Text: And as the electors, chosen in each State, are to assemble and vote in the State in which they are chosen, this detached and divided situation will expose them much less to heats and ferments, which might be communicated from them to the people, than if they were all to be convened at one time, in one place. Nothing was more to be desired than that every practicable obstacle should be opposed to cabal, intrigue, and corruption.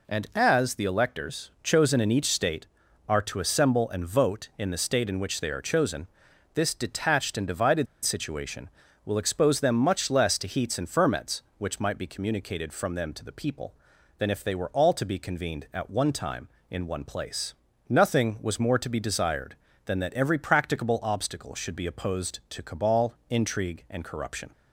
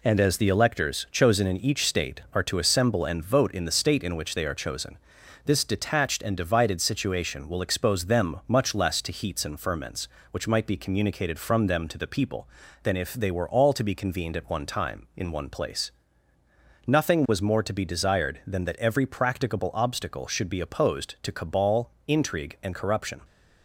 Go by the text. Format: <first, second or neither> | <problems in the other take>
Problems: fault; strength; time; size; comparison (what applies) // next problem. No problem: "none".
second | pauses between "divided" and "situation"; slight; at 7.8 s; 0.17 s long